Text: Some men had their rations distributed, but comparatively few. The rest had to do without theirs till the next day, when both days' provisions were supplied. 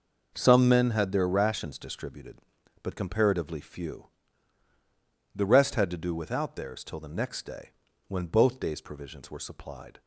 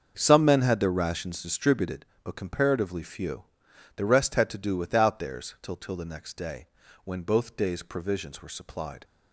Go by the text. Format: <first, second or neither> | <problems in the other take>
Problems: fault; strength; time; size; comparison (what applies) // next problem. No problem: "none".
first | starts louder than the rest; until 1.1 s; 6.5 dB // says "till" twice; at 5.7 s